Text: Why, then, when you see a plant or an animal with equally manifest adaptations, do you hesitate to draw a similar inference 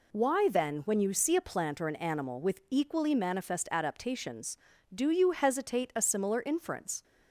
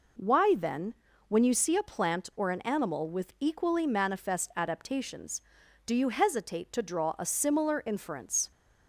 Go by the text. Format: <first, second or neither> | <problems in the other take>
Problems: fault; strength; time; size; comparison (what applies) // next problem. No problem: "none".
second | skips "to draw"; at 5.9 s